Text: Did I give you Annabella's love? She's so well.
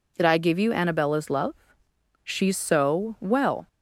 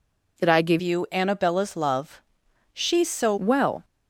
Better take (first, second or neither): first